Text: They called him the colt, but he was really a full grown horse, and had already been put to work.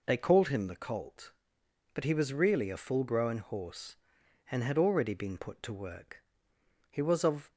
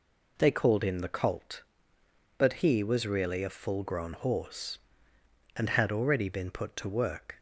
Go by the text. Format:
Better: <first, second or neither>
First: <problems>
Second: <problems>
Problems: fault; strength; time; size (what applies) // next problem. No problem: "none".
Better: second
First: goes on to say "He was of"; noticeable; from 6.8 s on; 0.62 s long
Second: none